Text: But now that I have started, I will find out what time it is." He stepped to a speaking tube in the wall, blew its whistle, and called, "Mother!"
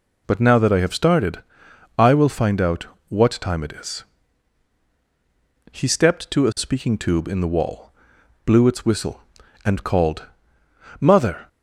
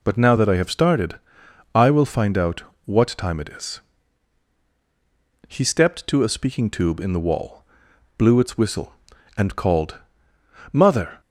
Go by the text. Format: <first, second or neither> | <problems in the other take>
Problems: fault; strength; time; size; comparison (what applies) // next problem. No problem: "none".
neither | pauses between "out" and "what"; slight; the same in both